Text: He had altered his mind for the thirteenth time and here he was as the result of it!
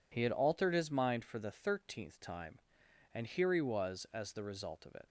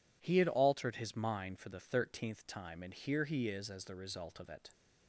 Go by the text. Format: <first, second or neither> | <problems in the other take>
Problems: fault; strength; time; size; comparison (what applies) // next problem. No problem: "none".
first | says "is" for "was"; at 3.4 s